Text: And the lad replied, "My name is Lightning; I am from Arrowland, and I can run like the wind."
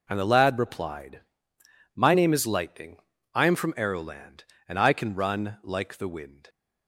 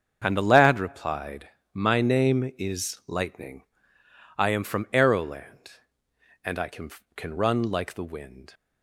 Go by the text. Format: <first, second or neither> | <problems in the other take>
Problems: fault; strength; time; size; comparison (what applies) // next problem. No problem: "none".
first | starts louder than the rest; until 1.2 s; 7 dB // says "can" twice; at 7.1 s